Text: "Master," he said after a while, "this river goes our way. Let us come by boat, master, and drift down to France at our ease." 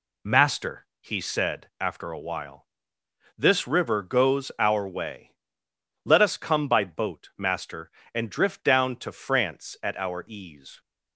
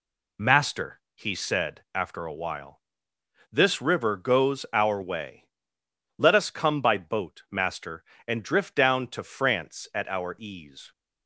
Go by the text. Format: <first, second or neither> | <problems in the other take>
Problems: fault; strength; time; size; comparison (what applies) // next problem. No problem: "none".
neither | none